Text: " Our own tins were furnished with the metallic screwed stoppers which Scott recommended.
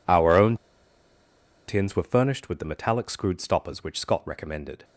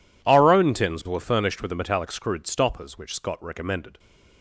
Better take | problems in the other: second | pauses between "own" and "tins"; at 0.5 s; 1.1 s long

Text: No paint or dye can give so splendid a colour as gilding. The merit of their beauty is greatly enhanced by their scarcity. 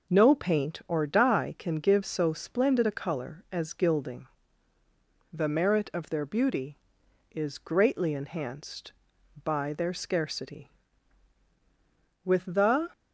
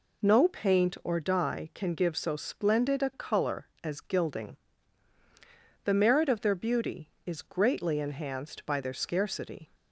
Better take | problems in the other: second | goes on to say "With the"; noticeable; from 12.2 s on; 0.66 s long

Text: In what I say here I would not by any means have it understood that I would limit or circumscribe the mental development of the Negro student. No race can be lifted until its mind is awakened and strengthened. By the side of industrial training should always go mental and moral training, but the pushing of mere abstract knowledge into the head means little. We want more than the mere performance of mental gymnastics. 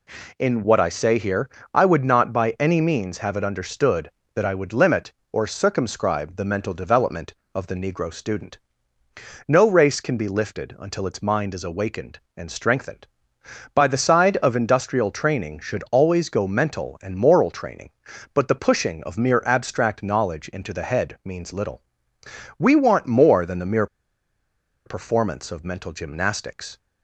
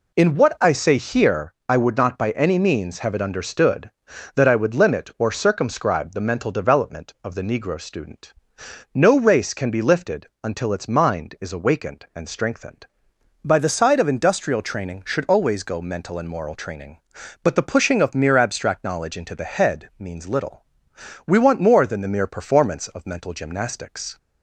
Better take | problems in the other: second | pauses between "here" and "I"; slight; at 1.4 s; 0.24 s long; slight in the second // pauses between "mere" and "performance"; at 23.8 s; 0.98 s long

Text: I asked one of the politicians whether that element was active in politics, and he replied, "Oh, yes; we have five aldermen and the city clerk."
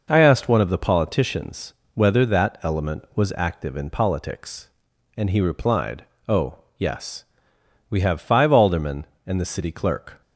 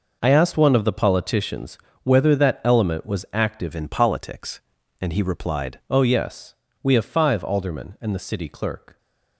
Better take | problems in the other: first | pauses between "politicians" and "whether"; slight; at 1.7 s; 0.26 s long; slight in the first // changes voice from "in" to "replied"; from 3.7 to 5.7 s; 2.0 s long

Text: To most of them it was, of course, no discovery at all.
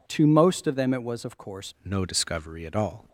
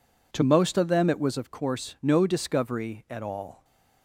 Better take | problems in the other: second | changes voice at "no"; from 1.8 s on; 1.2 s long

